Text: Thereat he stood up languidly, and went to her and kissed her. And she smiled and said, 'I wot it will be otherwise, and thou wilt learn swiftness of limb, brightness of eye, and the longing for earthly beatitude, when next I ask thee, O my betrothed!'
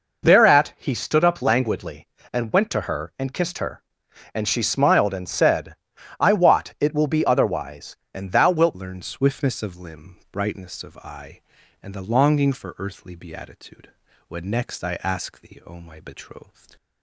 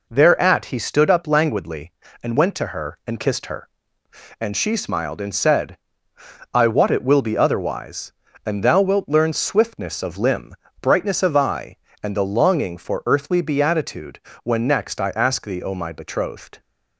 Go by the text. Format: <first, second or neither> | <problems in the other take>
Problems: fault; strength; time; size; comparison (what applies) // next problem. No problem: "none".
second | changes voice at "learn"; from 8.7 s on; 8.0 s long